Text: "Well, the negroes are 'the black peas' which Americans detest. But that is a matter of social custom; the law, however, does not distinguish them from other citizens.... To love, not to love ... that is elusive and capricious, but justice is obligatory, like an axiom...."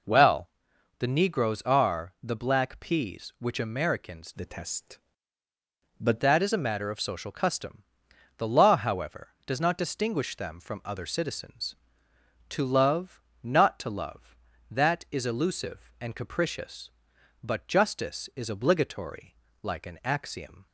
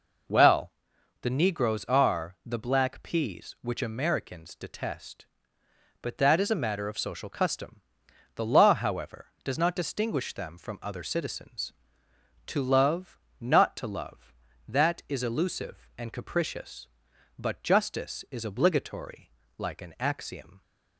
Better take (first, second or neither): second